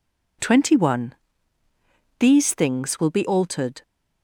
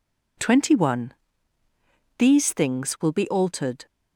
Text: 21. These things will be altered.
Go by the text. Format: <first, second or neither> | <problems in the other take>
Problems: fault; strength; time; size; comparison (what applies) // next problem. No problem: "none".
neither | none